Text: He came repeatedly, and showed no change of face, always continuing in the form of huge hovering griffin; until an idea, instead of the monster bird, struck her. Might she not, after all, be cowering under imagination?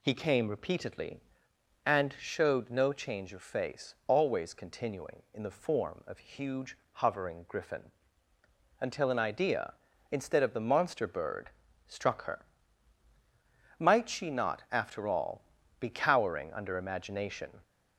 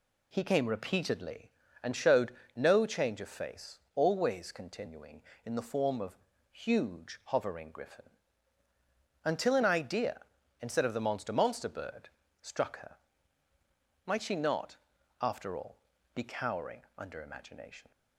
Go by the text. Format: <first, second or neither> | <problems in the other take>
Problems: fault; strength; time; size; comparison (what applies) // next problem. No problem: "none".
first | pauses between "showed" and "no"; slight; at 2.3 s; 0.22 s long // pauses between "of" and "huge"; slight; at 6.1 s; 0.34 s long // says "monster" twice; at 11.3 s